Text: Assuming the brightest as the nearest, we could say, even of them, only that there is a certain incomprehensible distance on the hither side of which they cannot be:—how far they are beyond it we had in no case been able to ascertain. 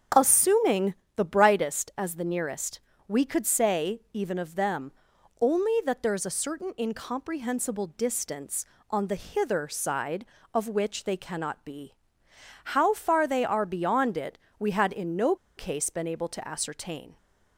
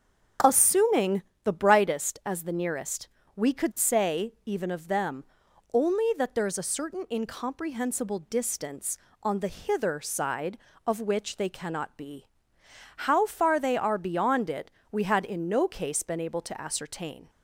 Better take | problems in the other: second | starts louder than the rest; strong; until 1.3 s; 7.5 dB; strong in the second // pauses between "Assuming" and "the"; slight; at 0.9 s; 0.22 s long; slight in the second // pauses between "it" and "we"; slight; at 14.3 s; 0.22 s long; slight in the second // pauses between "no" and "case"; slight; at 15.3 s; 0.22 s long

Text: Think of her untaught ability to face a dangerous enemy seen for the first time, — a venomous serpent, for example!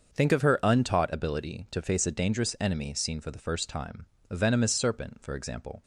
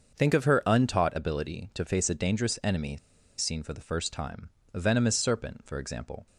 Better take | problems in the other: first | starts louder than the rest; until 1.2 s; 6.5 dB; also in the first // pauses between "enemy" and "seen"; at 2.9 s; 0.41 s long

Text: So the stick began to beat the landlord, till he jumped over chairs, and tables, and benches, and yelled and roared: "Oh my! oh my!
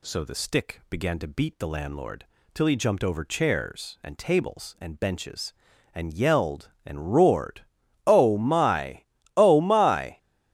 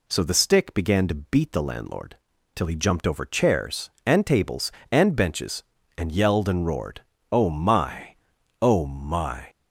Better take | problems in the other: neither | none

